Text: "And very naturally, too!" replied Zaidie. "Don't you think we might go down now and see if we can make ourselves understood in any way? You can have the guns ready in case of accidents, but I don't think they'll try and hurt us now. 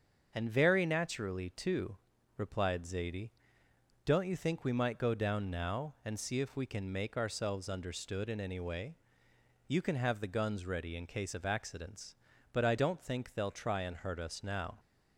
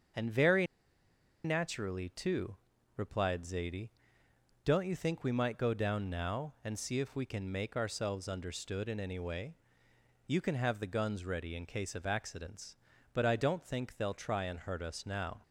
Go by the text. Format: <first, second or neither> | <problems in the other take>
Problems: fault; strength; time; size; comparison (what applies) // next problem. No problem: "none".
first | starts louder than the rest; until 1.9 s; 7 dB; also in the first // pauses between "very" and "naturally"; noticeable; at 0.6 s; 0.78 s long